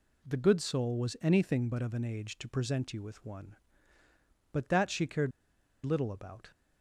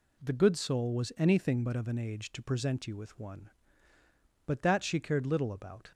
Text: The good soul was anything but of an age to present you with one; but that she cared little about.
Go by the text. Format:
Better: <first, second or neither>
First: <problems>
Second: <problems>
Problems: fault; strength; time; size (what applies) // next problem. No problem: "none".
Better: second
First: pauses between "cared" and "little"; noticeable; at 5.3 s; 0.53 s long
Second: none